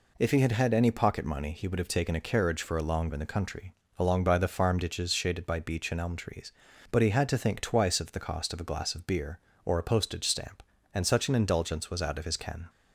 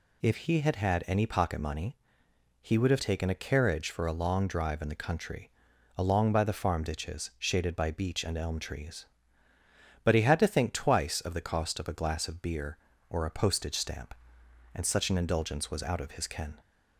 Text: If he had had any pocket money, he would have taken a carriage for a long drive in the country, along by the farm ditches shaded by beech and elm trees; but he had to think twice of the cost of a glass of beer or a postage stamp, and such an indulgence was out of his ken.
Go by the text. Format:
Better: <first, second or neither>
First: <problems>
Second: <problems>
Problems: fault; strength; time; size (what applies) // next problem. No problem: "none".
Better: second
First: skips "drive"; at 3.1 s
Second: none